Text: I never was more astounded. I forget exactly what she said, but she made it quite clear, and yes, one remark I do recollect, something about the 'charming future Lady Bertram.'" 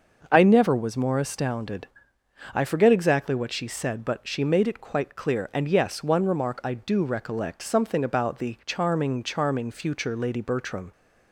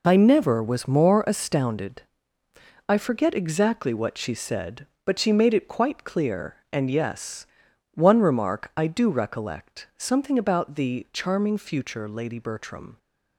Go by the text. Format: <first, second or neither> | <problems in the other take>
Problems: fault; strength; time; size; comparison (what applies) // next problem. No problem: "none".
second | starts louder than the rest; noticeable; until 1.3 s; 6 dB // says "charming" twice; at 9.2 s